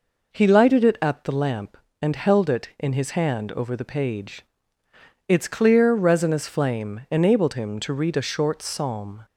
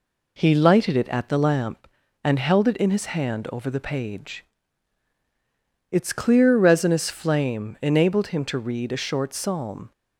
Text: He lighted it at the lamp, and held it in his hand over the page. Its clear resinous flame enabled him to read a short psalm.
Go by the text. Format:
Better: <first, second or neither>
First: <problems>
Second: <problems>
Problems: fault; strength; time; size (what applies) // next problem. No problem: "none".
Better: neither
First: none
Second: none